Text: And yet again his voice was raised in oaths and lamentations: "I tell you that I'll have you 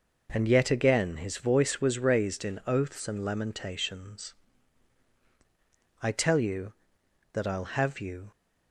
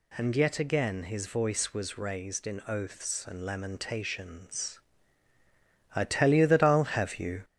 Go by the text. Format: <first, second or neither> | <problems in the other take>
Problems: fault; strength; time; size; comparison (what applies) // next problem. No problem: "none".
first | gets louder; throughout; 3.5 dB